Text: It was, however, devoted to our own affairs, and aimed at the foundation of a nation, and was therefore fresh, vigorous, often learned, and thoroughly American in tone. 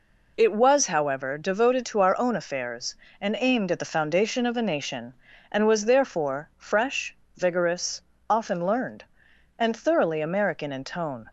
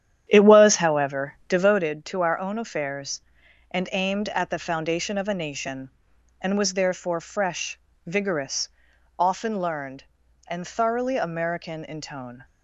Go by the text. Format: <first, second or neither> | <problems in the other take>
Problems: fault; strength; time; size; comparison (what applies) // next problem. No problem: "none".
first | starts louder than the rest; strong; until 1.9 s; 10 dB